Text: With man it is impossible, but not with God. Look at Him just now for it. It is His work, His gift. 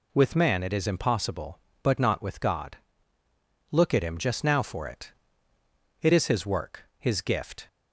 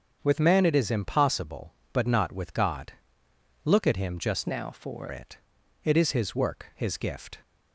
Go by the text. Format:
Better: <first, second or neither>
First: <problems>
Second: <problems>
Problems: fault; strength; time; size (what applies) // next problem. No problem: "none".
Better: first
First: none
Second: starts louder than the rest; until 1.2 s; 6.5 dB // changes voice from "now" to "for"; from 4.4 to 5.0 s; 0.6 s long